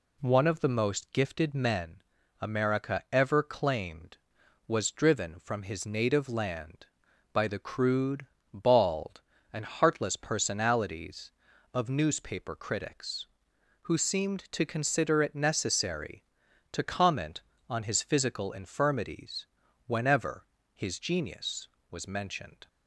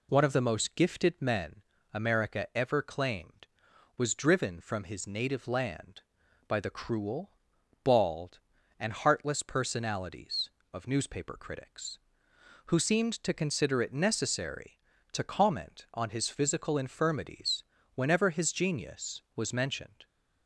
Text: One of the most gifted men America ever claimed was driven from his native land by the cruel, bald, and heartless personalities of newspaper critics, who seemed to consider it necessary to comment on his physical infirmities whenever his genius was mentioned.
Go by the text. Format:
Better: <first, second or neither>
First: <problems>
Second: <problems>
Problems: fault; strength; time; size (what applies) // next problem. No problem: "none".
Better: second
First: pauses between "men" and "America"; at 2.0 s; 0.40 s long // says "crude" for "cruel"; at 7.5 s // pauses between "infirmities" and "whenever"; at 19.4 s; 0.42 s long // pauses between "whenever" and "his"; slight; at 20.4 s; 0.32 s long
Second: pauses between "men" and "America"; slight; at 1.6 s; 0.32 s long // pauses between "infirmities" and "whenever"; slight; at 17.6 s; 0.32 s long